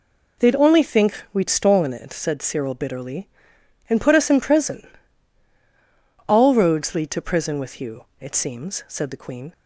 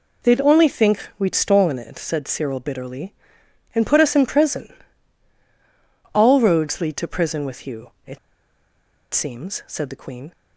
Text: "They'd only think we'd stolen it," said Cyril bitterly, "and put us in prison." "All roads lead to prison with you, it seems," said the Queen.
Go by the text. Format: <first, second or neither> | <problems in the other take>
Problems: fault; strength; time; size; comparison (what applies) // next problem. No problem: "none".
first | pauses between "it" and "seems"; noticeable; at 8.1 s; 0.94 s long